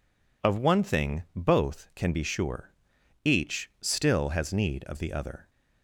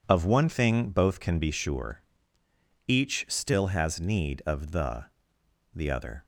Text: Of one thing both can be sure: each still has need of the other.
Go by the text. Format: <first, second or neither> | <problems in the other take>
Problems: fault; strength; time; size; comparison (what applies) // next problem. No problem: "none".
first | says "the" twice; at 5.7 s